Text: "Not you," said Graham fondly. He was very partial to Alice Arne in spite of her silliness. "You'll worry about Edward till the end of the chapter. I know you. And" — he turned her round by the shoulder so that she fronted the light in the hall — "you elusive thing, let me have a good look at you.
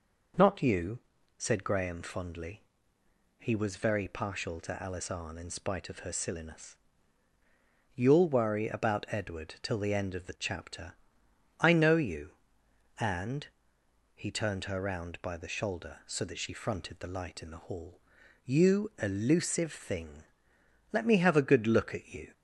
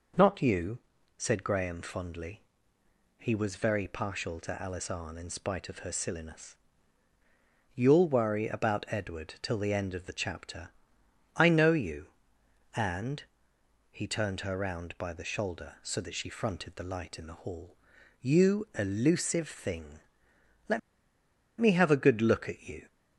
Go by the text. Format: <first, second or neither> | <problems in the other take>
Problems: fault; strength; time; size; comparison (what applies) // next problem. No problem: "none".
first | pauses between "let" and "me"; noticeable; at 20.7 s; 0.79 s long